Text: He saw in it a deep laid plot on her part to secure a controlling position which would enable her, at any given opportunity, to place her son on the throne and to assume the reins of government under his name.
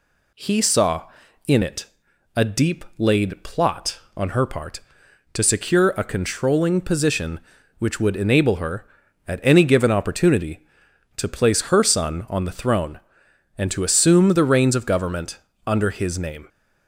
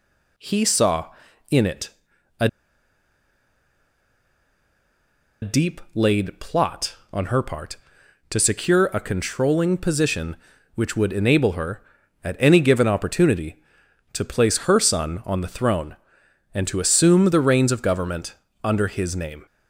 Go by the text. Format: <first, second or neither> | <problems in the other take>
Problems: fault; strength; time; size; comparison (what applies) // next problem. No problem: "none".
first | pauses between "it" and "a"; noticeable; at 1.8 s; 0.50 s long; noticeable in the first // pauses between "a" and "deep"; strong; at 2.4 s; 2.9 s long // pauses between "government" and "under"; slight; at 18.3 s; 0.30 s long; slight in the first